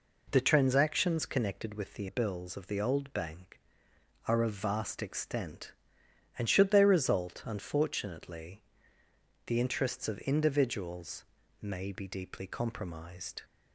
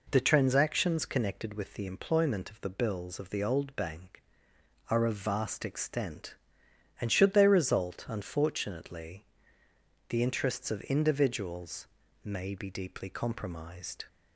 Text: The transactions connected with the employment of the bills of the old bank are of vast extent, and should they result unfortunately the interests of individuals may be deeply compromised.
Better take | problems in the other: second | skips "employment of the"; at 2.0 s // pauses between "unfortunately" and "the"; noticeable; at 8.6 s; 0.82 s long; noticeable in the second // pauses between "individuals" and "may"; slight; at 11.2 s; 0.36 s long; slight in the second

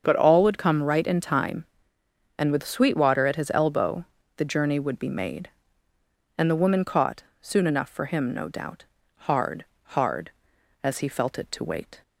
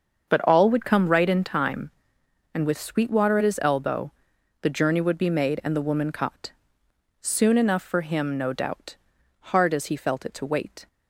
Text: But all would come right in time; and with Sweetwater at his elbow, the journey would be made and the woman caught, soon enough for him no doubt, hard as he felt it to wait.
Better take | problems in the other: second | starts louder than the rest; until 1.0 s; 7 dB; also in the second // says "hard" twice; at 9.9 s

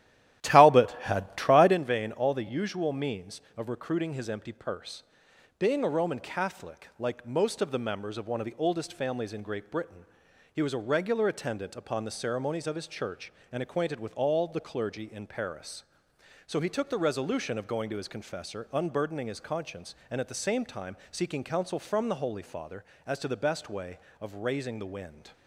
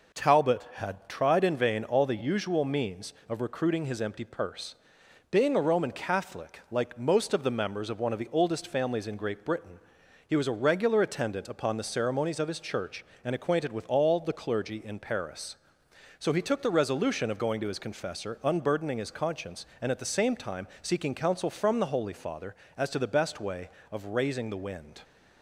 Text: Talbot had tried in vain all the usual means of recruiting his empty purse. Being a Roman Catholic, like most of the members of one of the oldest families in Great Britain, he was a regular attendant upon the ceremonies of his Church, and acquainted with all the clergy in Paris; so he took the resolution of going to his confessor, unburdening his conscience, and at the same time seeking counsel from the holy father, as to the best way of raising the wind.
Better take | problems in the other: second | starts louder than the rest; strong; until 1.8 s; 12.5 dB

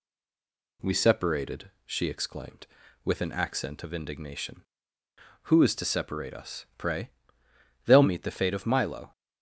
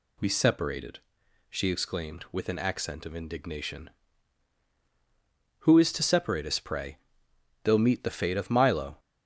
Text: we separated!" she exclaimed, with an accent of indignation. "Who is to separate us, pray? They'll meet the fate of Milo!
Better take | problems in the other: second | stays silent before the first word; slight; until 0.8 s; 0.8 s long

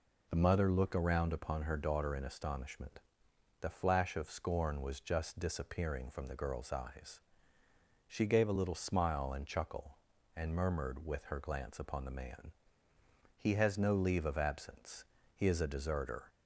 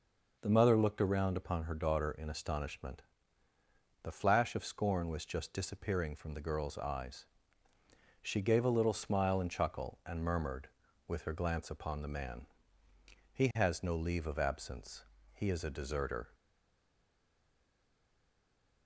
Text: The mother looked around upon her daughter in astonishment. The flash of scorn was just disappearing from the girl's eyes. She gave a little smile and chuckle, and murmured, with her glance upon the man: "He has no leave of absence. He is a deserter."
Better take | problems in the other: first | stays silent after the last word; from 16.3 s on; 2.5 s long

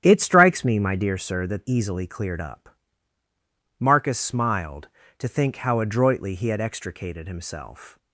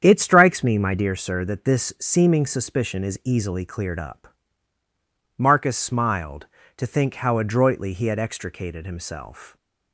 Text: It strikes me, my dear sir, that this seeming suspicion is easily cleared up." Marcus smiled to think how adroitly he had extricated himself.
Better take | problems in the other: second | starts louder than the rest; strong; until 1.0 s; 9.5 dB; strong in the second // skips "this seeming suspicion is"; at 1.6 s

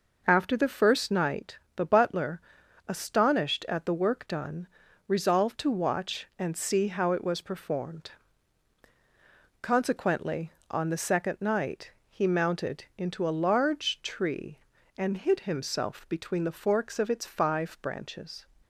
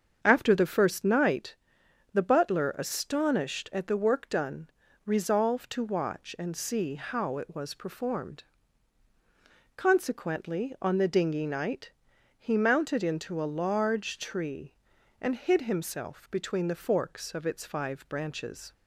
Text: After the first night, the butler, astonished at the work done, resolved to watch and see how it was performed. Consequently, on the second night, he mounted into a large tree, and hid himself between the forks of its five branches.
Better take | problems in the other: first | starts louder than the rest; strong; until 1.2 s; 7 dB // says "dinghy" for "second"; at 11.0 s

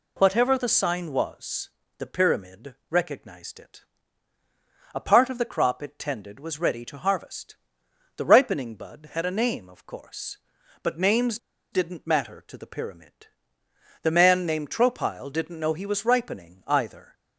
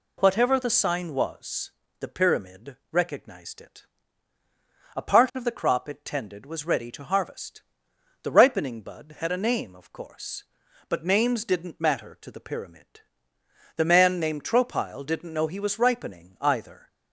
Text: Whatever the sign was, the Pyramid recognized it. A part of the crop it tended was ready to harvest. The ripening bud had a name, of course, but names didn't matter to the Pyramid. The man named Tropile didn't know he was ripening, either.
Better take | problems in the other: second | pauses between "Pyramid" and "recognized"; slight; at 2.7 s; 0.16 s long; slight in the second // pauses between "names" and "didn't"; slight; at 11.3 s; 0.34 s long

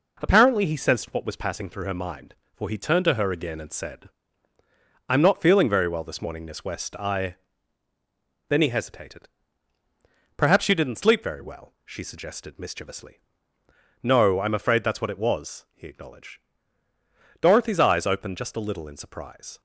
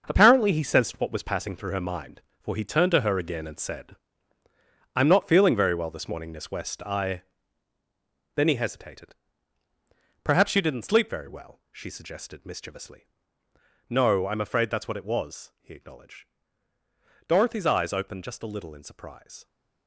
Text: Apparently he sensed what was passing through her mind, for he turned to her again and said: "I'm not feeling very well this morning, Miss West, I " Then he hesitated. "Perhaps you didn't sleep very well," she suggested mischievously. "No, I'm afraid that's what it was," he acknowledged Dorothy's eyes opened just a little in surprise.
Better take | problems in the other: first | gets quieter; strong; throughout; 8.5 dB // pauses between "acknowledged" and "Dorothy's"; at 16.2 s; 1.0 s long; also in the first

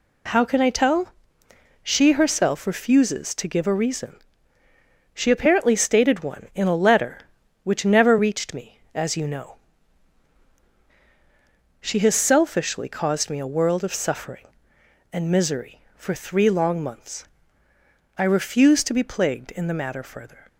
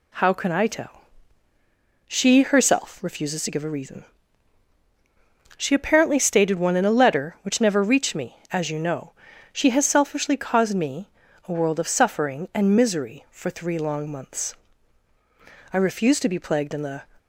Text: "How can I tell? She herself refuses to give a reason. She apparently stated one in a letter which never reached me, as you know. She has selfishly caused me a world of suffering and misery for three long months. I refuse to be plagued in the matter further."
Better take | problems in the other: first | pauses between "me" and "a"; at 11.0 s; 0.38 s long // stops before "matter further"; at 17.1 s

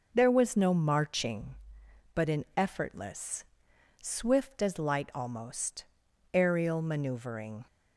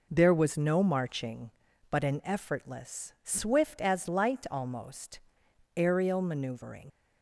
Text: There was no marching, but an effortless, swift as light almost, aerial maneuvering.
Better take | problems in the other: first | leaves "maneuvering" unfinished; at 6.8 s; 90 ms

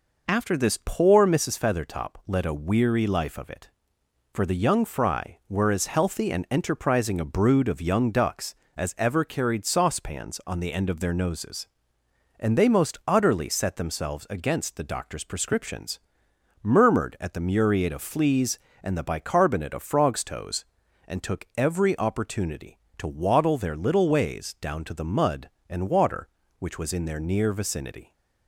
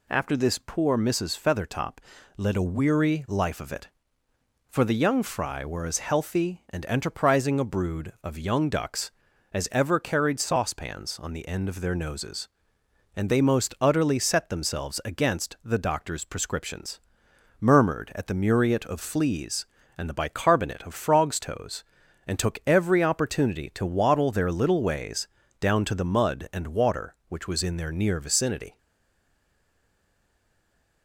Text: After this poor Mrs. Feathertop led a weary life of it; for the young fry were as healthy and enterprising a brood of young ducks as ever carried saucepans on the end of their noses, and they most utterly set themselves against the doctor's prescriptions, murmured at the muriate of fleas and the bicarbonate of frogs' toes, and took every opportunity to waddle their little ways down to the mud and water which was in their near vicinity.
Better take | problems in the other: first | pauses between "Feathertop" and "led"; at 1.9 s; 0.40 s long // pauses between "ways" and "down"; slight; at 25.2 s; 0.32 s long // stays silent after the last word; from 28.7 s on; 2.3 s long

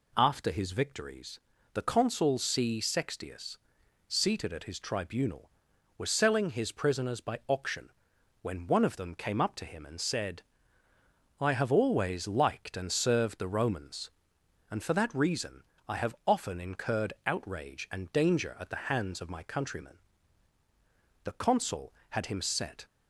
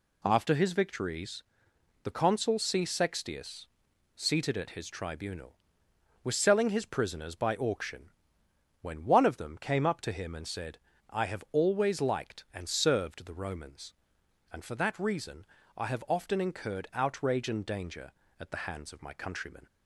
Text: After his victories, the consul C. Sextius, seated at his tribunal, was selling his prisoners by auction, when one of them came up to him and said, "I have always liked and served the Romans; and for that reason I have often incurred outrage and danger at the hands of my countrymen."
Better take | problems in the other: second | pauses between "reason" and "I"; slight; at 15.6 s; 0.24 s long; slight in the second // goes on to say "The consul had him set"; from 21.2 s on; 1.6 s long

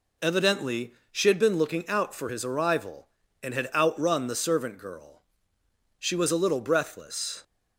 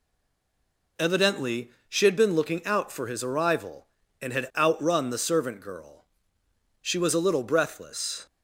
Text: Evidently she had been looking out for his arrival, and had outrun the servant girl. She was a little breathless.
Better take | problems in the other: first | stays silent before the first word; until 0.9 s; 0.9 s long // pauses between "Evidently" and "she"; slight; at 1.6 s; 0.18 s long; slight in the first

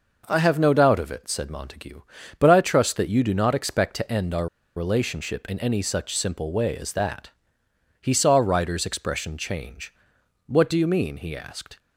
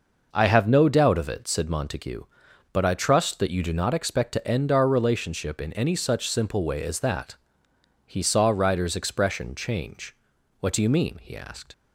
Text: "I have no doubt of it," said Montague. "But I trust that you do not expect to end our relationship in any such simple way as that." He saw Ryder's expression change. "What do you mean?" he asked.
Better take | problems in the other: second | pauses between "our" and "relationship"; slight; at 4.4 s; 0.27 s long

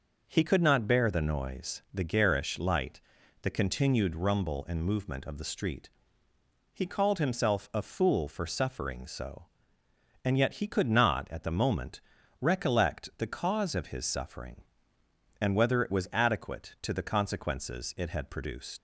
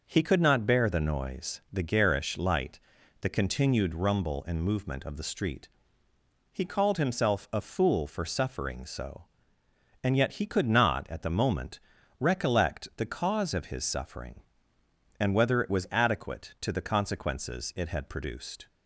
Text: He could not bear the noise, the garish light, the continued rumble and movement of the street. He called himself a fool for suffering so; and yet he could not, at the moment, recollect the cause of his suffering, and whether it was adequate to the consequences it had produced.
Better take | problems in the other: second | leaves "produced" unfinished; at 18.7 s; 95 ms

